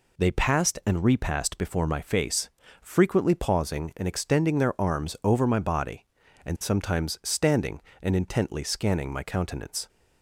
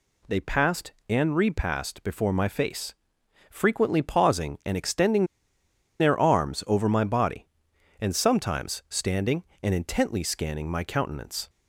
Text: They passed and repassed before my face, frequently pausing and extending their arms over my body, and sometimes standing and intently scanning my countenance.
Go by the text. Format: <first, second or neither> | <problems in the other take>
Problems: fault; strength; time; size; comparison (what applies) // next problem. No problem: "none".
first | pauses between "extending" and "their"; noticeable; at 5.2 s; 0.74 s long